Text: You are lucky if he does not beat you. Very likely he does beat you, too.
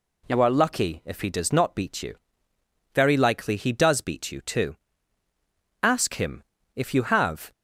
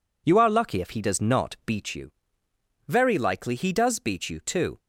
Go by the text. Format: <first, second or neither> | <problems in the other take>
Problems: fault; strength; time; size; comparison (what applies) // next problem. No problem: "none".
second | goes on to say "Ask him if you have"; strong; from 5.8 s on; 1.7 s long